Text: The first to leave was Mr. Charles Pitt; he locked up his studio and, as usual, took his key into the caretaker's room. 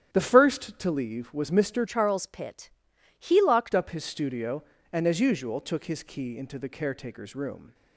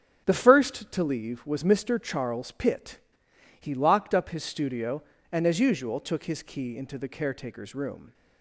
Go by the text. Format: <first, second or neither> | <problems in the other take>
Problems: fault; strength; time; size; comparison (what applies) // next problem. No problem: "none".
second | starts louder than the rest; strong; until 1.1 s; 10 dB; strong in the second // changes voice from "Charles" to "locked"; from 1.8 to 3.7 s; 1.9 s long